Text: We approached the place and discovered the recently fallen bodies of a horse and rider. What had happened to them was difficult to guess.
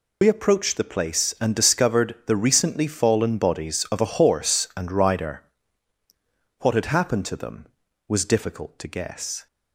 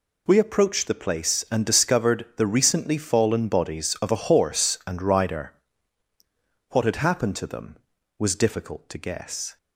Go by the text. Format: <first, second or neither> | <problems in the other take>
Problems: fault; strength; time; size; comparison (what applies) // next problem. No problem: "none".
second | loses the start of "We"; at 0.2 s; 50 ms